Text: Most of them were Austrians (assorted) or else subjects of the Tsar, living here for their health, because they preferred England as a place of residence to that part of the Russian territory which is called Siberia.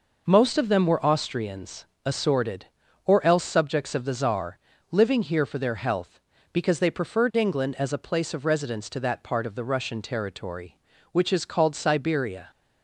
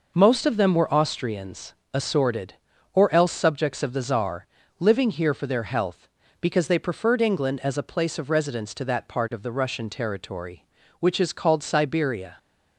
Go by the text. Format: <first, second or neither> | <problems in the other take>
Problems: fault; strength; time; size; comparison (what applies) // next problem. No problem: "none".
neither | none